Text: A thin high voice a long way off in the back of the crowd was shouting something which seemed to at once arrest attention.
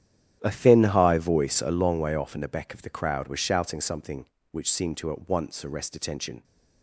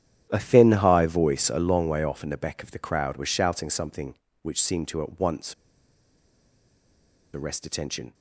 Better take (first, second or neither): first